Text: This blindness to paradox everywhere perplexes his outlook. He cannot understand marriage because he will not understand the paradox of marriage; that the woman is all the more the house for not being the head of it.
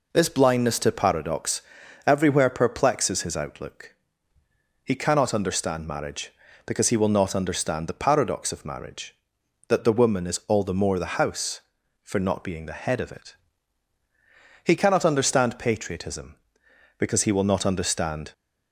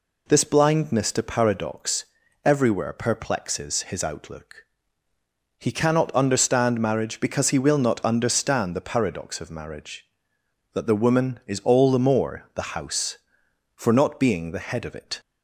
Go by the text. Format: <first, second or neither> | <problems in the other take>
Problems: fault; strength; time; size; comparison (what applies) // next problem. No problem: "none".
second | pauses between "paradox" and "everywhere"; at 1.6 s; 0.44 s long; also in the second // goes on to say "He cannot understand patriotism because he will not understand"; strong; from 14.6 s on; 3.6 s long